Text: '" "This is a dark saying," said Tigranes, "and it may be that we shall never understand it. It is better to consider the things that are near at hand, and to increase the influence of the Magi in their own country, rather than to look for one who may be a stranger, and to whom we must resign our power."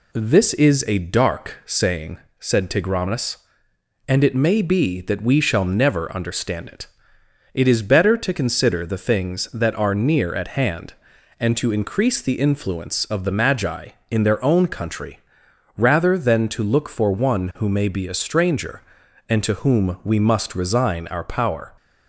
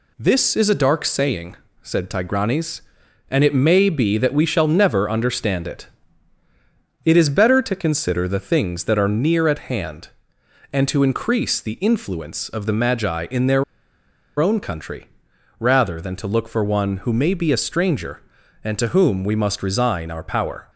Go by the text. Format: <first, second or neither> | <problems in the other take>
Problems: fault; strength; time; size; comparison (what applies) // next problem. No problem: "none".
first | pauses between "their" and "own"; noticeable; at 13.6 s; 0.75 s long